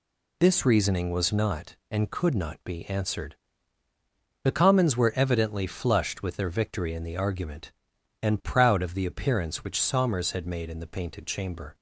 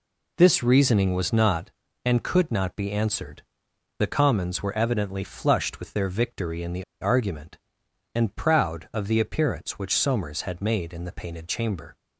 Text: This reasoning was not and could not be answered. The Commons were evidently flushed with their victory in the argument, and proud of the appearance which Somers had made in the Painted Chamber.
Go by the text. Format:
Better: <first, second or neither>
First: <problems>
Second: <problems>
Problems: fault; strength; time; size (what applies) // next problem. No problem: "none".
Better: first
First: none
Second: pauses between "the" and "argument"; slight; at 6.8 s; 0.17 s long